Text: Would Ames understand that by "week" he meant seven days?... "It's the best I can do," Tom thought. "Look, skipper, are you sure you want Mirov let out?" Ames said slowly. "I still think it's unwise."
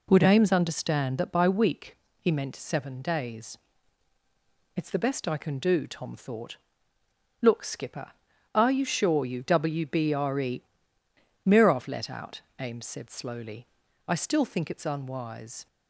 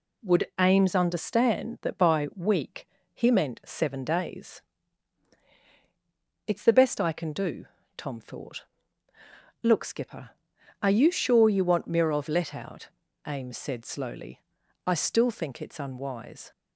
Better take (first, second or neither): second